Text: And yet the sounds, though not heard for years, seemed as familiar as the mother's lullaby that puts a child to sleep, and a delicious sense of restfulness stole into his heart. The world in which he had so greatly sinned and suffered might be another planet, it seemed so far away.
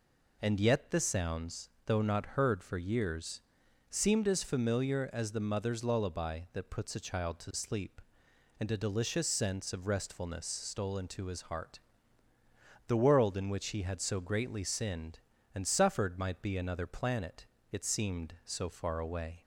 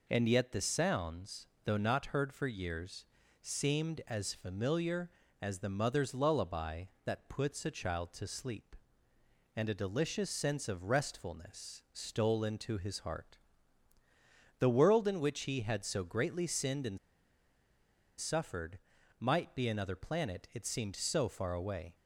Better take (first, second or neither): first